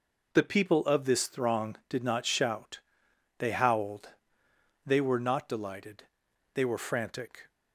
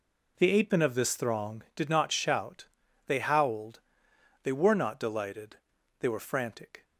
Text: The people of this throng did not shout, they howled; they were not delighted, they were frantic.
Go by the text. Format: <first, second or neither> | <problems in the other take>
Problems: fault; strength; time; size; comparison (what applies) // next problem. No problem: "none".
first | says "apemen" for "people"; at 0.5 s